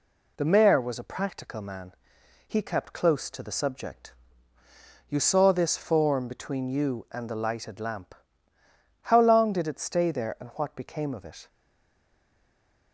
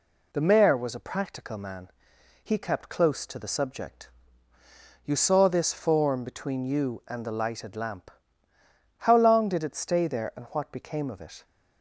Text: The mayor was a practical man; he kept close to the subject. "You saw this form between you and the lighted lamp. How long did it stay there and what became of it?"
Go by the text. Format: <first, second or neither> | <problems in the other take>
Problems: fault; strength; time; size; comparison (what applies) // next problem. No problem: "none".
second | stays silent after the last word; noticeable; from 11.4 s on; 1.5 s long